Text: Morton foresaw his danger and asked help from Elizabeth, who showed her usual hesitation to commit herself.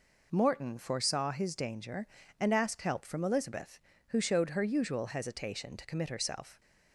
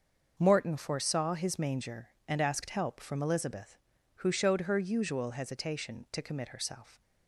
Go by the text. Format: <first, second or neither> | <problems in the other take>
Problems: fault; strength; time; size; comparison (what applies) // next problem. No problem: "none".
first | starts louder than the rest; until 1.3 s; 6.5 dB // says "manger" for "danger"; at 1.5 s